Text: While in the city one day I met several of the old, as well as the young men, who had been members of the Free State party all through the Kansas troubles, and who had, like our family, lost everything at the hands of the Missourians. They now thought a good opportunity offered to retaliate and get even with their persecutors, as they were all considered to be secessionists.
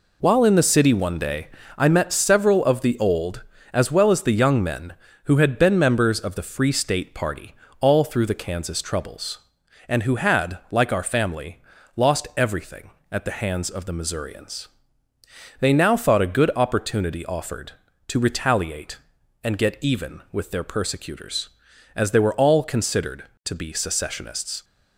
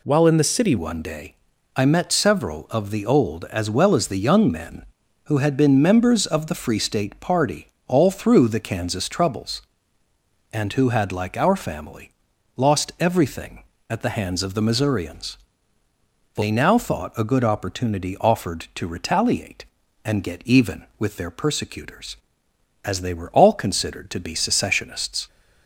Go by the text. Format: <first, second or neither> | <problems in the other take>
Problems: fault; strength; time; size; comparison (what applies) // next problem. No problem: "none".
first | changes voice at "one"; from 0.7 s on; 24.5 s long // pauses between "day" and "I"; at 1.3 s; 0.42 s long; slight in the first // pauses between "party" and "all"; slight; at 7.6 s; 0.22 s long; slight in the first